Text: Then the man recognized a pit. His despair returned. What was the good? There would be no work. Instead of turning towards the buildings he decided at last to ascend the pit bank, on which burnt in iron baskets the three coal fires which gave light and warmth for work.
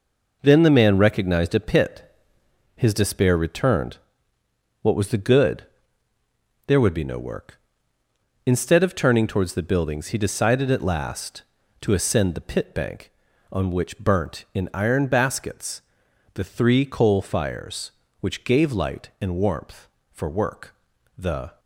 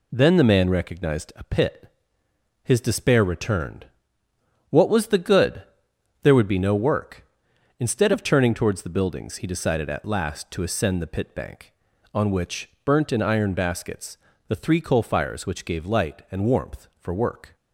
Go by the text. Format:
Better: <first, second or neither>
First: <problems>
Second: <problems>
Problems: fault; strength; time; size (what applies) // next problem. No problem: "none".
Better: second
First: pauses between "baskets" and "the"; noticeable; at 15.8 s; 0.54 s long // goes on to say "The"; slight; from 21.1 s on; 0.42 s long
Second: pauses between "baskets" and "the"; slight; at 14.1 s; 0.32 s long